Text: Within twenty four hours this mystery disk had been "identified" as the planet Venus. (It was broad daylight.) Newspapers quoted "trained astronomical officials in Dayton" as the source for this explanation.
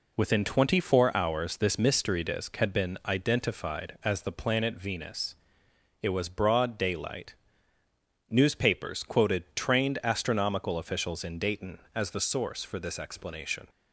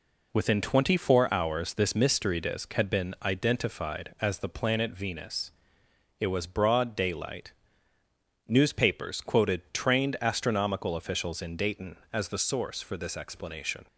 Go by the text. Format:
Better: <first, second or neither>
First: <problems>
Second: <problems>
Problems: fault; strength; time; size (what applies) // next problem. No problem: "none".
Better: neither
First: none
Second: none